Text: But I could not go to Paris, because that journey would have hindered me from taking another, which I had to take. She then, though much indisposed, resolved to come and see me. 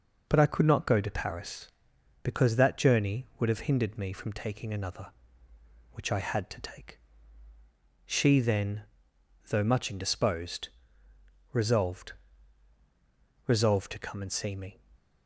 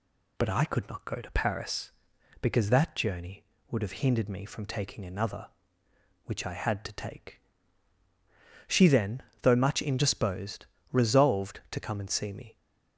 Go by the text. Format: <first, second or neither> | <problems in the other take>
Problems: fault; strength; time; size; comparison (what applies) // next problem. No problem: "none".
second | says "resolved" twice; at 13.4 s